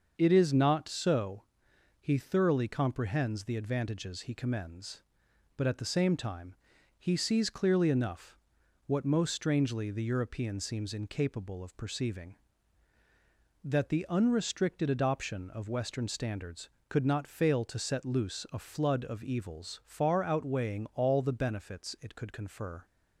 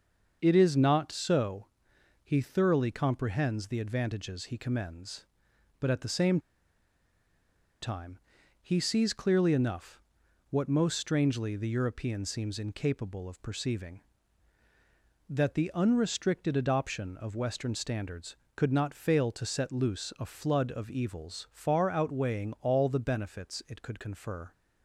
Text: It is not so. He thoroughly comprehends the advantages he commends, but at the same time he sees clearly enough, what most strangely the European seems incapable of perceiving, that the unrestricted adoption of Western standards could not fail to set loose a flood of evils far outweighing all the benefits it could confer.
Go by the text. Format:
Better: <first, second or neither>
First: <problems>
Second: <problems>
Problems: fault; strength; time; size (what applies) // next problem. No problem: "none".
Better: first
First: starts louder than the rest; until 1.1 s; 6.5 dB // pauses between "time" and "he"; at 6.5 s; 0.44 s long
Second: starts louder than the rest; until 1.4 s; 6.5 dB // pauses between "same" and "time"; strong; at 6.3 s; 1.4 s long // pauses between "time" and "he"; at 8.1 s; 0.44 s long